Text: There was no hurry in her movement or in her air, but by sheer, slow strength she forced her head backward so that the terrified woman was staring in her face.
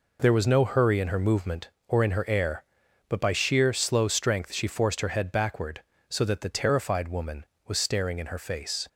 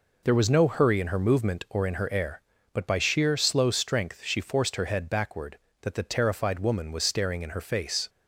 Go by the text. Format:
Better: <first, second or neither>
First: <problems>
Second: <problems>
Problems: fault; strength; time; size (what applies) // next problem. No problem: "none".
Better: first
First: none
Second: skips "so"; at 5.6 s